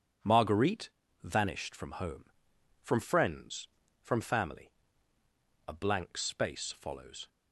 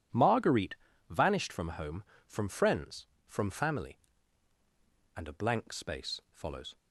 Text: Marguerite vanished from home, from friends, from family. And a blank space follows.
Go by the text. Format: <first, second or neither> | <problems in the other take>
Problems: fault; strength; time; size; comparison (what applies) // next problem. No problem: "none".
second | pauses between "Marguerite" and "vanished"; slight; at 0.8 s; 0.34 s long; slight in the second // skips "And"; at 5.2 s